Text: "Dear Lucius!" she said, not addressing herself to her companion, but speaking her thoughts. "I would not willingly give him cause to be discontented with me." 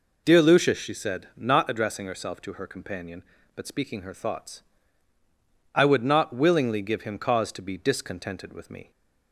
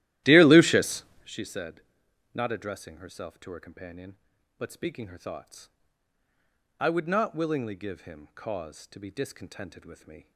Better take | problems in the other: first | starts louder than the rest; strong; until 1.4 s; 14.5 dB

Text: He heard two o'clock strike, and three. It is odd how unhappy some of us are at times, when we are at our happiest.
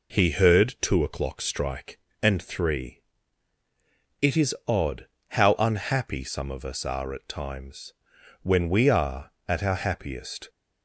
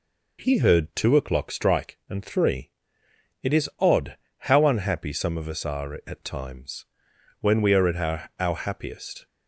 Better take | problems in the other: first | pauses between "odd" and "how"; slight; at 4.1 s; 0.22 s long; slight in the first // says "our" twice; at 8.3 s

